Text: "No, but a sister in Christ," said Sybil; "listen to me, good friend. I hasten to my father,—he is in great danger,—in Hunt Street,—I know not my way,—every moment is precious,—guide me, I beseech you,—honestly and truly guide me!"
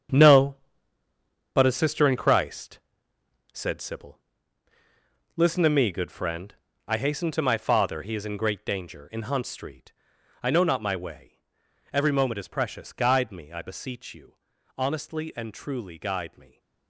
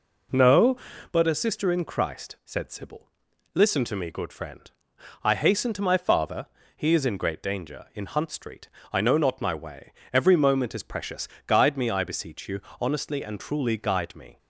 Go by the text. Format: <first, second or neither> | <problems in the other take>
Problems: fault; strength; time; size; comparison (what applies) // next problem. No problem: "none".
second | gets quieter; strong; throughout; 11 dB